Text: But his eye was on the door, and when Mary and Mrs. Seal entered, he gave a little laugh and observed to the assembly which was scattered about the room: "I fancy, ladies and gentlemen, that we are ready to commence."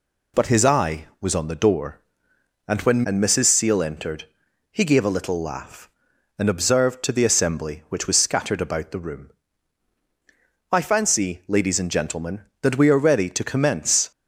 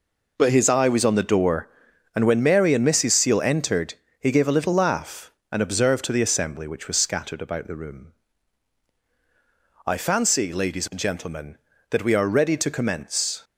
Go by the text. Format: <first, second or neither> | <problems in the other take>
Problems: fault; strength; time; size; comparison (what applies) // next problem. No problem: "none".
second | skips "Mary"; at 3.0 s